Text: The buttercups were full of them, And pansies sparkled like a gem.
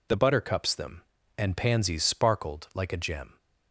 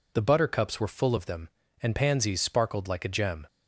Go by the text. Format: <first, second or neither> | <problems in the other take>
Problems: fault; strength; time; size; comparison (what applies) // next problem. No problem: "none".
second | skips "were full of"; at 0.7 s